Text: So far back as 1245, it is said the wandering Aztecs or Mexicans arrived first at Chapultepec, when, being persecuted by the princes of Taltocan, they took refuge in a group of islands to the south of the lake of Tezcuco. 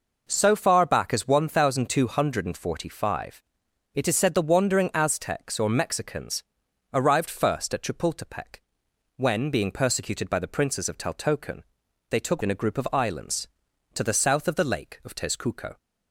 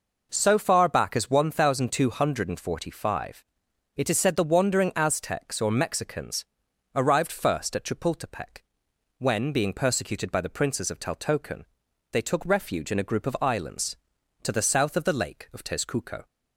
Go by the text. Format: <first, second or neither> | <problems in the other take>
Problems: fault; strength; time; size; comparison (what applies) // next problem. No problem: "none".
second | pauses between "Mexicans" and "arrived"; noticeable; at 6.4 s; 0.48 s long; noticeable in the second // skips "refuge"; at 12.4 s